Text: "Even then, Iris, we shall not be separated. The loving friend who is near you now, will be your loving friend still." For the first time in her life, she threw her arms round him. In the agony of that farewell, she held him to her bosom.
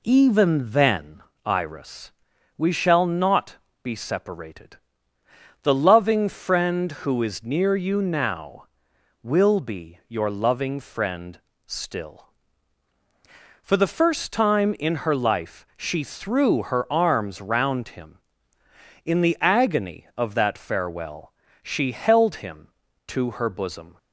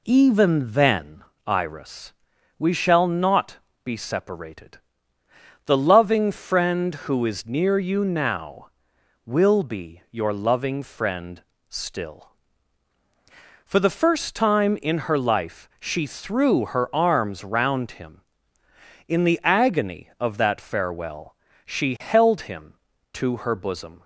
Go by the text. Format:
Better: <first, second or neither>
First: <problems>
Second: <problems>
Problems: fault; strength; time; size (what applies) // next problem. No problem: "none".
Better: neither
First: pauses between "not" and "be"; slight; at 3.5 s; 0.26 s long // pauses between "friend" and "still"; slight; at 11.3 s; 0.28 s long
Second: pauses between "not" and "be"; slight; at 3.5 s; 0.26 s long // pauses between "friend" and "still"; slight; at 11.4 s; 0.28 s long